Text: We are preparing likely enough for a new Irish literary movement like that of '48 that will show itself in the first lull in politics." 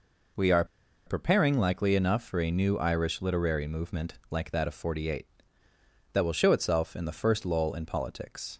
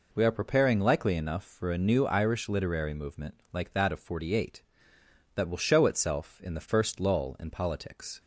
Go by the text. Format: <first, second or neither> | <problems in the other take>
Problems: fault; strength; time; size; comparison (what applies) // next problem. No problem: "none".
second | pauses between "are" and "preparing"; at 0.6 s; 0.42 s long // pauses between "movement" and "like"; slight; at 4.1 s; 0.18 s long